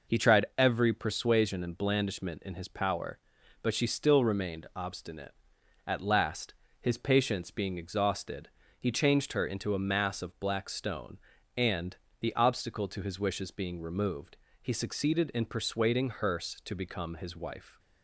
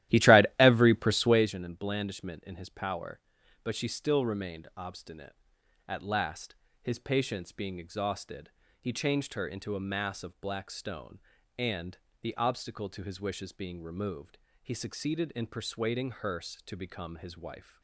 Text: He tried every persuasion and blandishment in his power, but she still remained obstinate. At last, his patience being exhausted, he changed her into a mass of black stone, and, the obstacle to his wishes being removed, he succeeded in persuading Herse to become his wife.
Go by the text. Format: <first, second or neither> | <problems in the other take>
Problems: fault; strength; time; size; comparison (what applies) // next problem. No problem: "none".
first | starts louder than the rest; strong; until 1.6 s; 14 dB